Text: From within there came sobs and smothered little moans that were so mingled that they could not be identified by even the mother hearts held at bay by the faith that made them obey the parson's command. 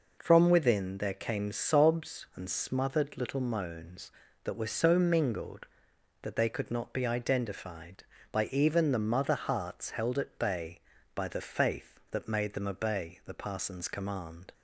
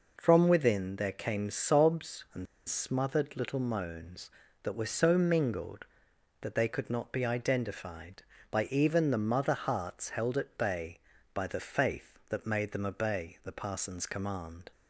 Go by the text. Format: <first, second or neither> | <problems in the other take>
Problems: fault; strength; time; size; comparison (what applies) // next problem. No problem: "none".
first | pauses between "and" and "smothered"; slight; at 2.4 s; 0.23 s long